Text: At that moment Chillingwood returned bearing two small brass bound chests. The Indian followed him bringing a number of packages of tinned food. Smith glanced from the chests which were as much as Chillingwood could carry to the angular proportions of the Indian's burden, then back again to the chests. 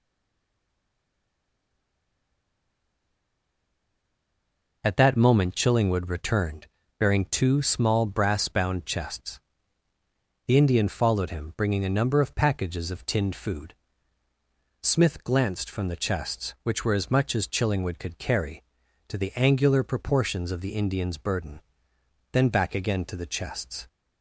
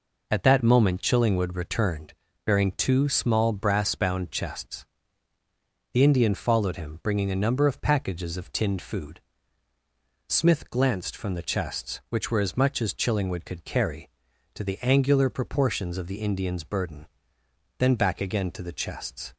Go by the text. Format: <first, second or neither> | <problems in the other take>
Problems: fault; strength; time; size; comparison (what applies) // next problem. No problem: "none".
second | stays silent before the first word; strong; until 4.8 s; 4.8 s long // pauses between "returned" and "bearing"; slight; at 6.6 s; 0.32 s long; slight in the second